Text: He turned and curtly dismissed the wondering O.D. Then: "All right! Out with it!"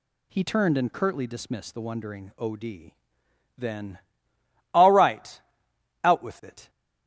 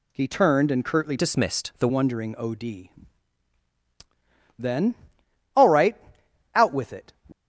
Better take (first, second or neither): first